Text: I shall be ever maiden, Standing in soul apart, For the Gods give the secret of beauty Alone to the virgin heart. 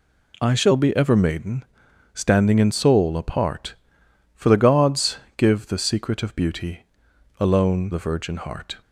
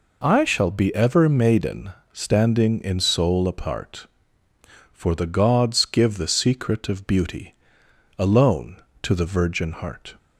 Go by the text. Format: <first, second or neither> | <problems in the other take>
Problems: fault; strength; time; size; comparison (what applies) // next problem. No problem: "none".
second | pauses between "Gods" and "give"; slight; at 5.1 s; 0.18 s long // pauses between "beauty" and "Alone"; noticeable; at 6.8 s; 0.56 s long; noticeable in the second // skips "to"; at 7.9 s